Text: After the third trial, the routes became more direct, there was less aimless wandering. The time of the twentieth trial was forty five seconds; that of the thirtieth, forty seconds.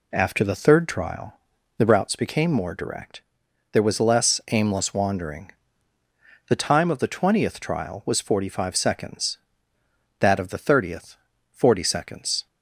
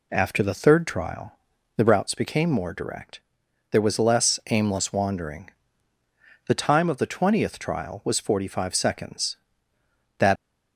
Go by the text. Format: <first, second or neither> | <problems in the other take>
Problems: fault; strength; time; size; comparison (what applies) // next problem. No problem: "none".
first | stops before "of the thirtieth forty seconds"; at 10.3 s